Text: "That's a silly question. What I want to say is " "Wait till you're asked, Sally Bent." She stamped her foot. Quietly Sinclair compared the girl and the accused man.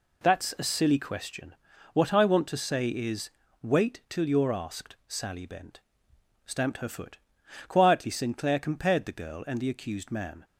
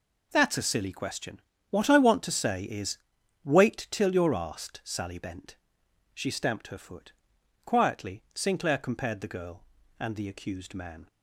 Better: second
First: skips "She"; at 6.1 s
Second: none

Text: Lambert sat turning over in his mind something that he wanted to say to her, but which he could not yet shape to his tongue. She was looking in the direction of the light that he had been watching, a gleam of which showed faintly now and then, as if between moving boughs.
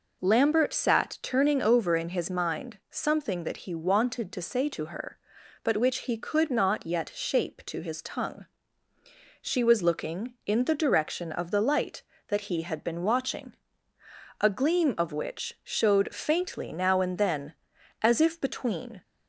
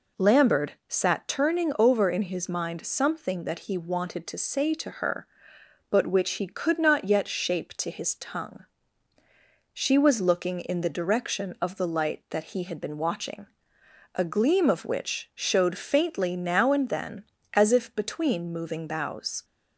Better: second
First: stops before "moving boughs"; at 19.0 s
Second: none

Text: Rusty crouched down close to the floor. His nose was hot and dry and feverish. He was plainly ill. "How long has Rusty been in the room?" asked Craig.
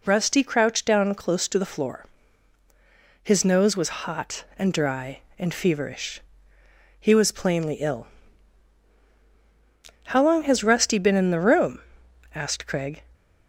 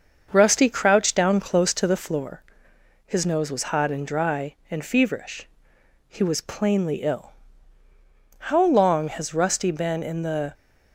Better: first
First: none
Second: starts louder than the rest; until 1.3 s; 6.5 dB // stops before "room asked Craig"; at 10.5 s

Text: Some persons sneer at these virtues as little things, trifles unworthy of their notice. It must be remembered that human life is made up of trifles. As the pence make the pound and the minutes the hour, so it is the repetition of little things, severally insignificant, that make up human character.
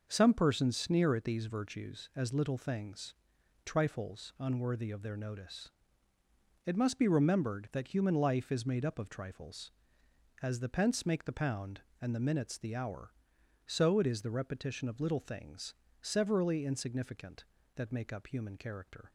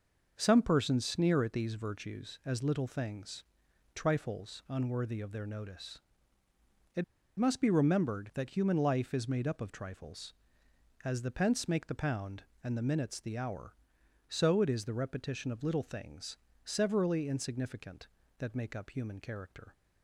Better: first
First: starts louder than the rest; noticeable; until 1.1 s; 6 dB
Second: starts louder than the rest; noticeable; until 1.3 s; 6 dB // pauses between "It" and "must"; slight; at 7.0 s; 0.34 s long

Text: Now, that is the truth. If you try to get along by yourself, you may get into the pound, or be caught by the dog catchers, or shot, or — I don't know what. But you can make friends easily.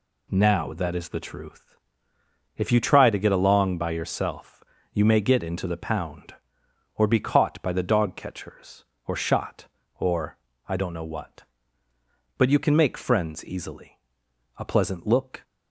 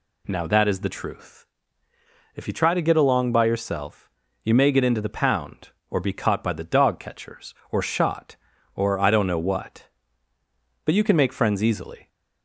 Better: second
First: goes on to say "A pleasant look"; noticeable; from 14.5 s on; 0.86 s long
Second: none

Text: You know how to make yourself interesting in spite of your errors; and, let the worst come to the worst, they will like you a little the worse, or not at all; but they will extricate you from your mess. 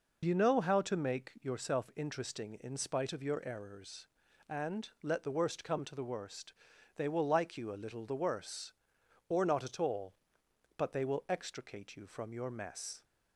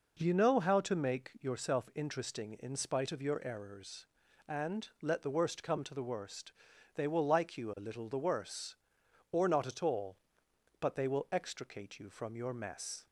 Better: second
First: loses the start of "You"; at 0.2 s; 50 ms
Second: none

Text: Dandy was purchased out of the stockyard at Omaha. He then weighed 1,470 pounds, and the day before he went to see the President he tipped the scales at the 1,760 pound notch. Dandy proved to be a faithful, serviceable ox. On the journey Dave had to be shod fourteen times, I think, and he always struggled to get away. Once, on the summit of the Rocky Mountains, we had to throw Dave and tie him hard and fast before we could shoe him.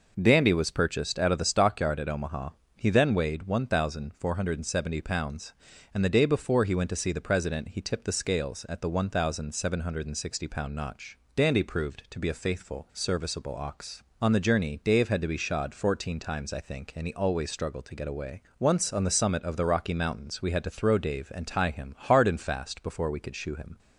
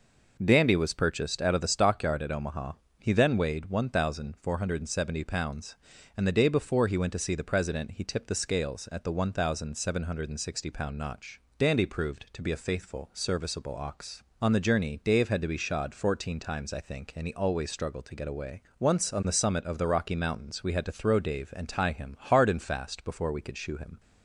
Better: neither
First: none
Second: none

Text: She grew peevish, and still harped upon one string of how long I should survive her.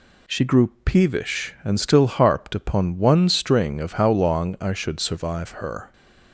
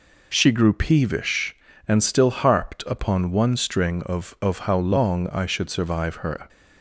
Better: first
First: none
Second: says "of" twice; at 4.4 s

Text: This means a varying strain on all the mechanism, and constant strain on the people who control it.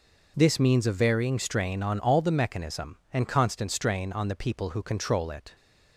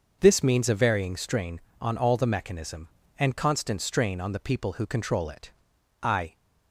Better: first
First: none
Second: starts louder than the rest; noticeable; until 1.2 s; 6 dB // goes on to say "I"; slight; from 6.0 s on; 0.36 s long

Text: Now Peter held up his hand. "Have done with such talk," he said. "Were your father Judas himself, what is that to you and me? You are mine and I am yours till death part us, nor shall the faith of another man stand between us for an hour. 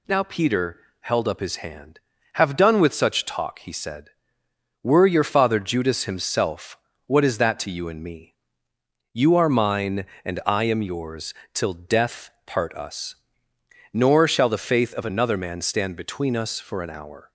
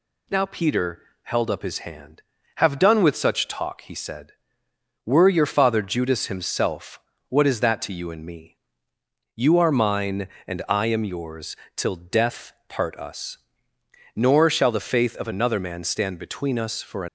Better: first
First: pauses between "Peter" and "held"; slight; at 0.7 s; 0.22 s long // pauses between "yours" and "till"; slight; at 11.3 s; 0.20 s long // pauses between "death" and "part"; slight; at 12.2 s; 0.16 s long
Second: pauses between "Peter" and "held"; slight; at 1.0 s; 0.22 s long // pauses between "yours" and "till"; slight; at 11.5 s; 0.20 s long // pauses between "death" and "part"; slight; at 12.5 s; 0.16 s long // stops before "hour"; at 17.0 s

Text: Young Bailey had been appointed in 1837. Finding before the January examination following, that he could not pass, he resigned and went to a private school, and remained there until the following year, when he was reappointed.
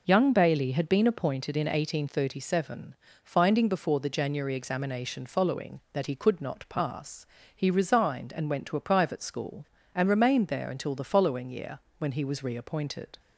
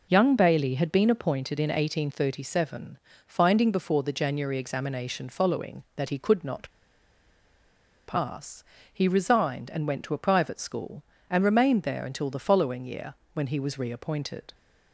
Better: first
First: none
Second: pauses between "not" and "pass"; strong; at 6.7 s; 1.3 s long

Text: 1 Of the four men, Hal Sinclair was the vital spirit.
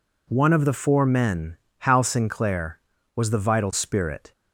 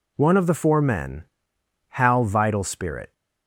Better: first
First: none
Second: skips "Sinclair was the"; at 2.2 s

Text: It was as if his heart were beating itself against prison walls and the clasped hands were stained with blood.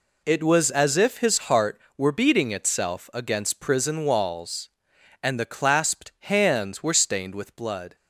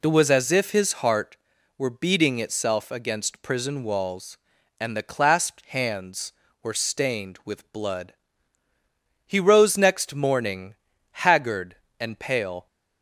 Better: first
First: none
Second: goes on to say "He rose next morning haggard and pale"; strong; from 9.2 s on; 3.4 s long

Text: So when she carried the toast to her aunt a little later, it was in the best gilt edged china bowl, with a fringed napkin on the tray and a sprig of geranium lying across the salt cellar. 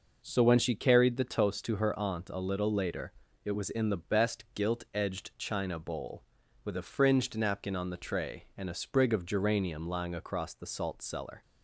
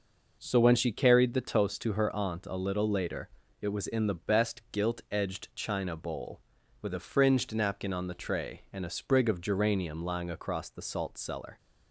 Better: neither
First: none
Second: none

